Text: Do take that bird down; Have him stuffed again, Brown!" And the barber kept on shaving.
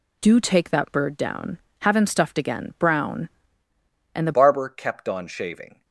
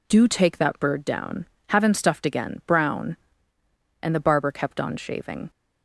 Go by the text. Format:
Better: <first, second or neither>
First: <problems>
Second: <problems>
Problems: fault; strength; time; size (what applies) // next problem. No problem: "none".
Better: second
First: changes voice at "barber"; from 4.3 s on; 1.5 s long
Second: none